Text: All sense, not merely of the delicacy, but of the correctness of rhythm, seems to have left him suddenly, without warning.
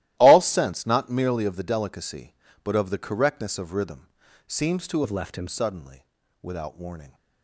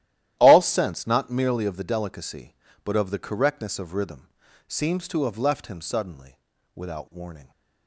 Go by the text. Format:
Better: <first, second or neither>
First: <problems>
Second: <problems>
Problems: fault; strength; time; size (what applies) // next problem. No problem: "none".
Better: second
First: starts louder than the rest; strong; until 1.1 s; 15 dB // changes voice from "have" to "him"; from 5.0 to 5.4 s; 0.4 s long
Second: starts louder than the rest; strong; until 1.4 s; 13 dB